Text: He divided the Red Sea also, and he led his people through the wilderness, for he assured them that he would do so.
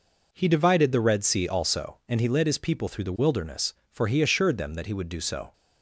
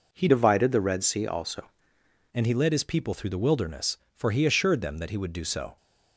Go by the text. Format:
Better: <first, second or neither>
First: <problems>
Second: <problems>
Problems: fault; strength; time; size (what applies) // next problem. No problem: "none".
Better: first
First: none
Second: changes voice from "divided" to "also"; from 0.2 to 1.7 s; 1.5 s long